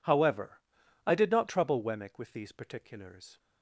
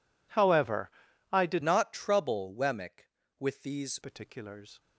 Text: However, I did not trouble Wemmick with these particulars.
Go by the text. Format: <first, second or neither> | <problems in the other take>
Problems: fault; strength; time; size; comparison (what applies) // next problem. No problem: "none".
first | changes voice from "not" to "these"; from 1.6 to 3.9 s; 2.3 s long